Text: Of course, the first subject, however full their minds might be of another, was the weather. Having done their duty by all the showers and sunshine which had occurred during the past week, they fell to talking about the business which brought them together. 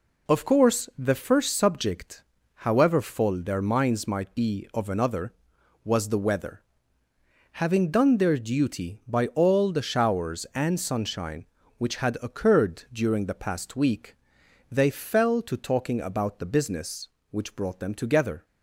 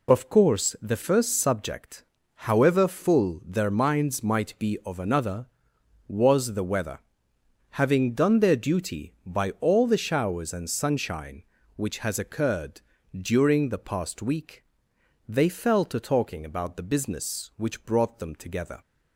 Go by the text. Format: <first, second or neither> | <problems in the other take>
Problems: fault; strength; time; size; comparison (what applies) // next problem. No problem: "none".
first | says "has" for "had"; at 11.9 s // pauses between "occurred" and "during"; slight; at 12.8 s; 0.34 s long